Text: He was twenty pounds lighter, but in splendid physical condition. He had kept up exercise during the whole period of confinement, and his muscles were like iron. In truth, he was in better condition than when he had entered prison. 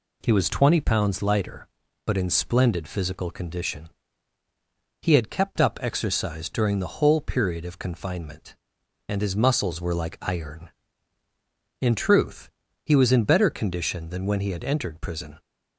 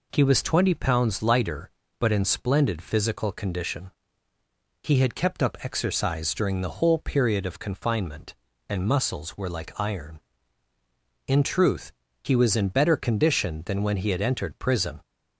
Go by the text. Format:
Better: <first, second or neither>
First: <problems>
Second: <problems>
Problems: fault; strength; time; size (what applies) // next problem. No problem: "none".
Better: first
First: none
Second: skips "his"; at 8.8 s